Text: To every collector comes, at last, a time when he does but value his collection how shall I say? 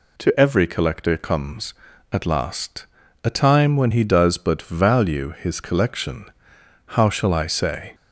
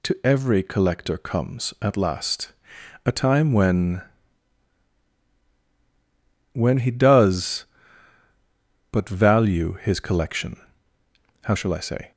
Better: first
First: pauses between "collection" and "how"; noticeable; at 6.2 s; 0.60 s long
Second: says "when" twice; at 6.5 s // pauses between "collection" and "how"; noticeable; at 10.5 s; 0.86 s long

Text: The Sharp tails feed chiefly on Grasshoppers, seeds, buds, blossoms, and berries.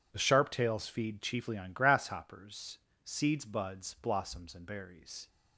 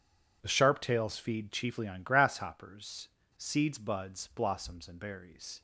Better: neither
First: none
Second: none

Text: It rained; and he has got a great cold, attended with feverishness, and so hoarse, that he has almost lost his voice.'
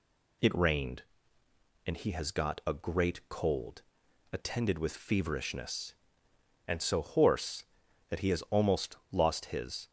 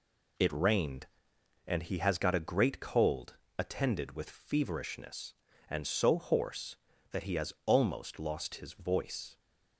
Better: second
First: pauses between "almost" and "lost"; slight; at 8.9 s; 0.16 s long // stops before "voice"; at 9.8 s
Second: none

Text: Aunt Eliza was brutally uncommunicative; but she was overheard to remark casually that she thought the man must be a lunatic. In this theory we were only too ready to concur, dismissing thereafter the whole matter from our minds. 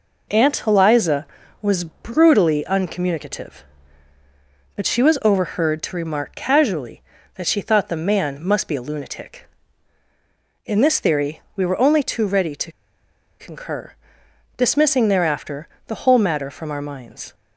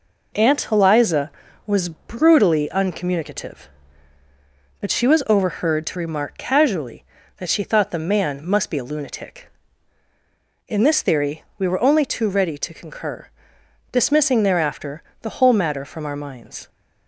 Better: second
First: pauses between "theory" and "we"; slight; at 11.3 s; 0.16 s long // pauses between "to" and "concur"; noticeable; at 12.7 s; 0.67 s long // pauses between "thereafter" and "the"; slight; at 15.6 s; 0.20 s long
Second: pauses between "theory" and "we"; slight; at 11.4 s; 0.16 s long // pauses between "thereafter" and "the"; slight; at 15.0 s; 0.20 s long

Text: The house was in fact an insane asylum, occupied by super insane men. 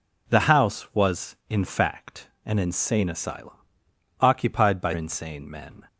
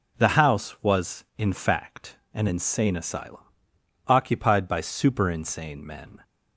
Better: second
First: skips "super"; at 4.9 s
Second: none

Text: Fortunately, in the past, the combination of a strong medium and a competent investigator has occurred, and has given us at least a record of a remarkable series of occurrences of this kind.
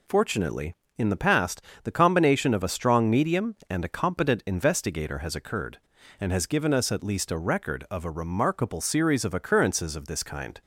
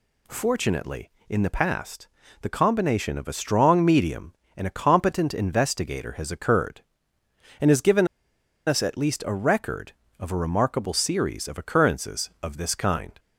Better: first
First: none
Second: pauses between "given" and "us"; noticeable; at 8.0 s; 0.59 s long

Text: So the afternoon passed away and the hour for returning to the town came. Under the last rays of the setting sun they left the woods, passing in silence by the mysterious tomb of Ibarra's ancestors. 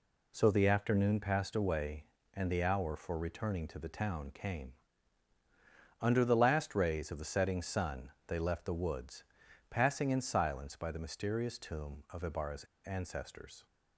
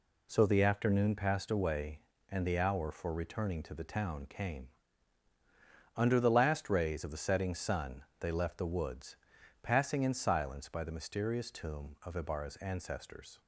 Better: second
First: pauses between "sun" and "they"; slight; at 8.1 s; 0.16 s long // pauses between "Ibarra's" and "ancestors"; slight; at 12.6 s; 0.20 s long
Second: pauses between "sun" and "they"; slight; at 8.0 s; 0.16 s long

